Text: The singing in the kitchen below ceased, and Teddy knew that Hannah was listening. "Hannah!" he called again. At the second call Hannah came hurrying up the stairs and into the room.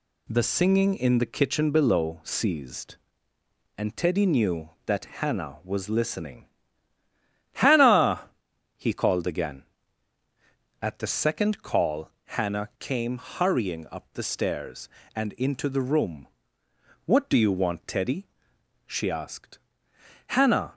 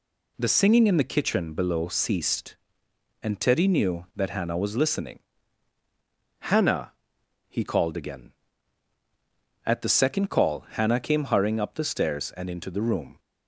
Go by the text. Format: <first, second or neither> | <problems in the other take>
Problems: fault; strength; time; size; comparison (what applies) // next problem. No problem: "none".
second | pauses between "that" and "Hannah"; slight; at 5.0 s; 0.16 s long // pauses between "call" and "Hannah"; slight; at 12.0 s; 0.26 s long // goes on to say "What do you want Teddy she asked Hannah"; strong; from 17.0 s on; 3.6 s long